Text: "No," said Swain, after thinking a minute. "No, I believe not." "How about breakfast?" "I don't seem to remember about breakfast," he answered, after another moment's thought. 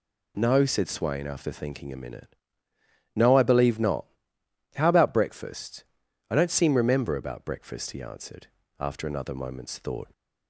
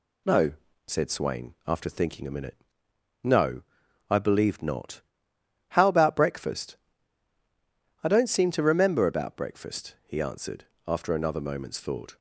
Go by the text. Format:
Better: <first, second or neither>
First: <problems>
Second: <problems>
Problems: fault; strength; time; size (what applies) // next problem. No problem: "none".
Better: second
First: skips "to"; at 6.7 s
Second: none